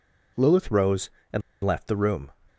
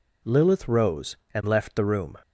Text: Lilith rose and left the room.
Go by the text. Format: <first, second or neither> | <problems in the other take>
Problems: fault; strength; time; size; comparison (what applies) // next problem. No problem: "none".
second | pauses between "and" and "left"; slight; at 1.4 s; 0.23 s long